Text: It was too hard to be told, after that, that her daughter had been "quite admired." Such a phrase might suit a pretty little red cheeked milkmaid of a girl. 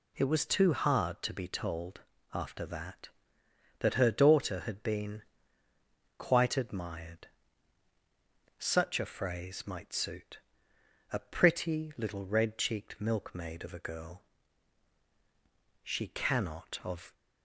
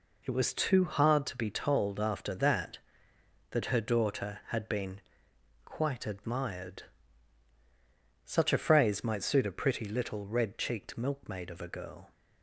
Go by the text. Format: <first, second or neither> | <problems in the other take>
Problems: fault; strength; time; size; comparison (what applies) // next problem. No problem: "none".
second | pauses between "been" and "quite"; noticeable; at 5.2 s; 0.94 s long; noticeable in the second // pauses between "suit" and "a"; noticeable; at 10.3 s; 0.74 s long // goes on to say "She cannot of"; from 15.8 s on; 1.3 s long